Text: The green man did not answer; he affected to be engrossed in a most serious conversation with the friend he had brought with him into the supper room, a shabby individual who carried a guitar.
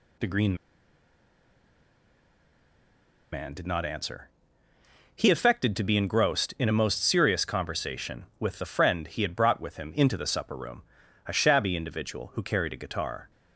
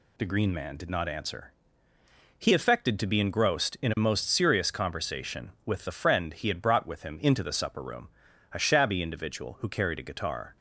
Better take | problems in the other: second | pauses between "green" and "man"; strong; at 0.5 s; 2.7 s long

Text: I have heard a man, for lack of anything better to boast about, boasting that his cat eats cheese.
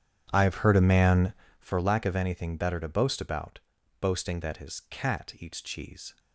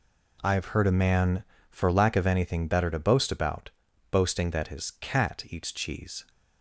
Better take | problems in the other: second | starts louder than the rest; strong; until 1.7 s; 9.5 dB

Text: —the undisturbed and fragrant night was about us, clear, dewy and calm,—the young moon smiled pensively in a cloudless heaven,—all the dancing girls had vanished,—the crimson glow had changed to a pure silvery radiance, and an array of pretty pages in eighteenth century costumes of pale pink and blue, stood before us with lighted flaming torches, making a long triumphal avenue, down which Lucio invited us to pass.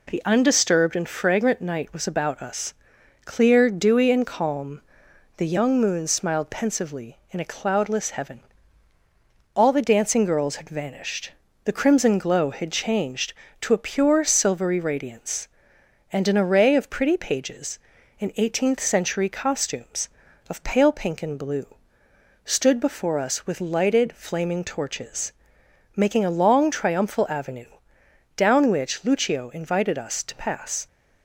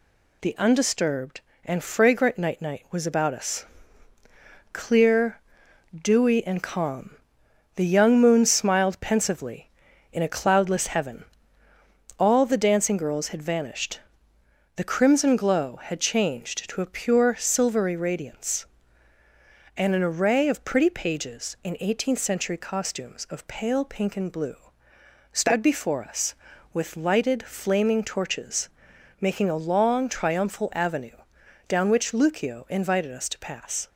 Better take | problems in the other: first | says "night" twice; at 2.6 s

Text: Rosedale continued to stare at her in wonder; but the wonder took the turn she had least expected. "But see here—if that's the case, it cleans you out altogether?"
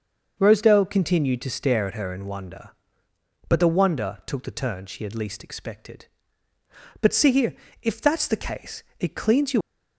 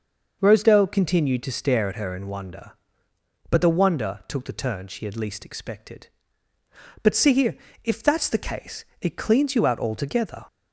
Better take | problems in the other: second | starts louder than the rest; noticeable; until 1.4 s; 6 dB // stops before "out altogether"; at 9.6 s

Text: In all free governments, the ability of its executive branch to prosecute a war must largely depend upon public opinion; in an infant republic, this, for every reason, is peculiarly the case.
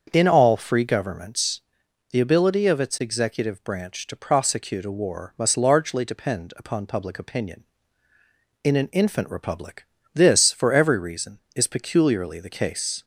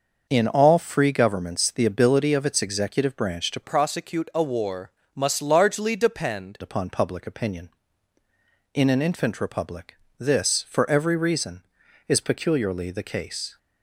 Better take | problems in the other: first | starts louder than the rest; noticeable; until 1.3 s; 6 dB; also in the first // changes voice from "prosecute" to "depend"; from 3.6 to 6.5 s; 2.9 s long // pauses between "war" and "must"; slight; at 4.8 s; 0.24 s long

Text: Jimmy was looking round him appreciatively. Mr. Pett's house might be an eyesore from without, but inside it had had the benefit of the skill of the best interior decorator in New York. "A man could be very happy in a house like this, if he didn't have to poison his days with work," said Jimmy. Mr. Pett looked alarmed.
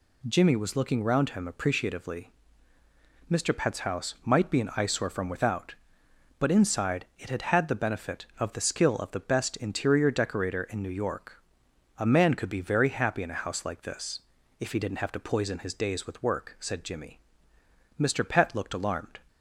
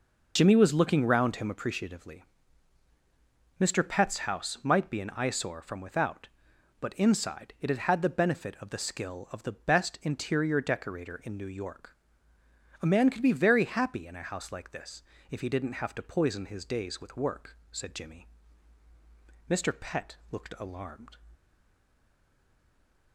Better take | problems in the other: first | stays silent after the last word; noticeable; from 21.3 s on; 1.8 s long

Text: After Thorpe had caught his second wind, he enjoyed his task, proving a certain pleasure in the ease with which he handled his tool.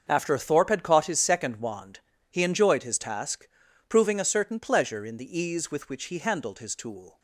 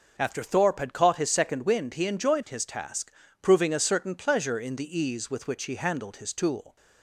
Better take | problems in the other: second | starts louder than the rest; until 1.0 s; 6.5 dB; noticeable in the second // says "wand" for "wind"; at 1.5 s

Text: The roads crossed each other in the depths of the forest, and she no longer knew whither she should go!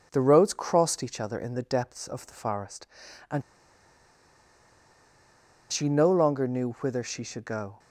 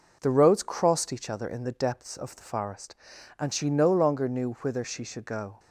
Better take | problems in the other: second | pauses between "and" and "she"; strong; at 3.4 s; 2.3 s long

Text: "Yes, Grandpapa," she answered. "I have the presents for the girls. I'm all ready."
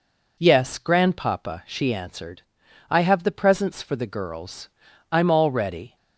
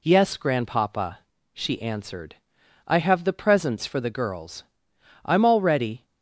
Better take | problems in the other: neither | none

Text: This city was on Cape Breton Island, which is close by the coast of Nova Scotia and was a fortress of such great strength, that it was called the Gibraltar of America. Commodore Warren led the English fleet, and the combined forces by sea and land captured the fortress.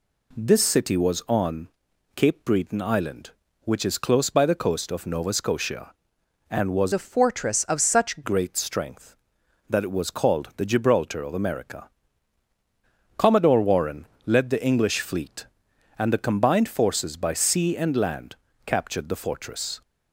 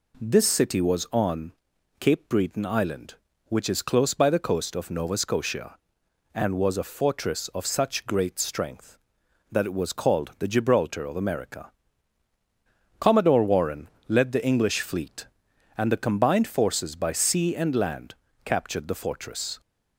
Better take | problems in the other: second | pauses between "on" and "Cape"; noticeable; at 1.6 s; 0.48 s long; noticeable in the second // changes voice from "a" to "such"; from 6.9 to 8.2 s; 1.3 s long // pauses between "Warren" and "led"; slight; at 14.0 s; 0.18 s long; slight in the second // pauses between "land" and "captured"; slight; at 18.3 s; 0.30 s long; slight in the second

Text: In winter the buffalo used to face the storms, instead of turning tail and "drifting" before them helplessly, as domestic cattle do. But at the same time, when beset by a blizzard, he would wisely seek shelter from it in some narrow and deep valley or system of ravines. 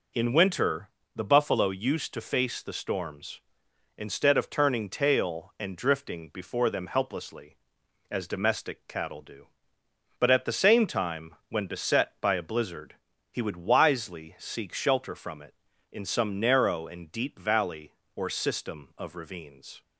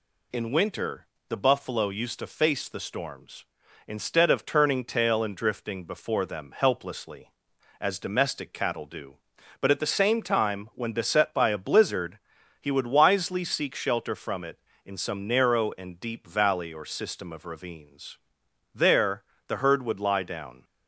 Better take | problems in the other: first | pauses between "winter" and "the"; slight; at 1.0 s; 0.22 s long; slight in the first // goes on to say "There the herd would lie down"; strong; from 18.7 s on; 1.9 s long

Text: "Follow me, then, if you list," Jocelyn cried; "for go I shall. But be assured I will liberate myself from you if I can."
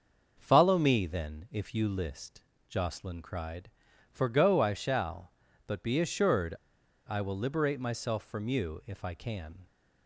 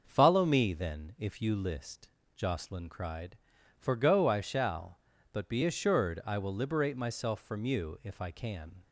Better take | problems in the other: second | starts louder than the rest; until 1.4 s; 6.5 dB; also in the second // pauses between "assured" and "I"; noticeable; at 6.5 s; 0.54 s long

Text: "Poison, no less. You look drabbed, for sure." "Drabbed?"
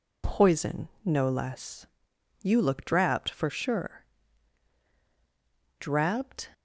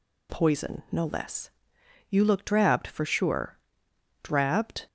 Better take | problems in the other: neither | none

